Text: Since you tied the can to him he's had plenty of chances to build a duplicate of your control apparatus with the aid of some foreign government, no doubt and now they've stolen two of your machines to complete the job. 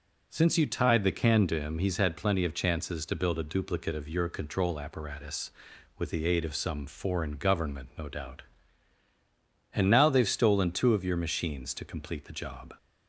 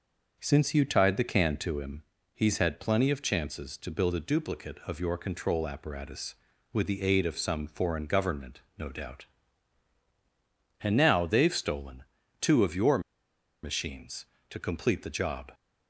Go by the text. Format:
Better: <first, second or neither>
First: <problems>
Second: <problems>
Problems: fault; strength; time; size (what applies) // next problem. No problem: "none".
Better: first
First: none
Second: starts louder than the rest; until 1.4 s; 6 dB // pauses between "him" and "he's"; slight; at 2.0 s; 0.32 s long // pauses between "stolen" and "two"; slight; at 12.0 s; 0.36 s long // pauses between "your" and "machines"; noticeable; at 12.9 s; 0.63 s long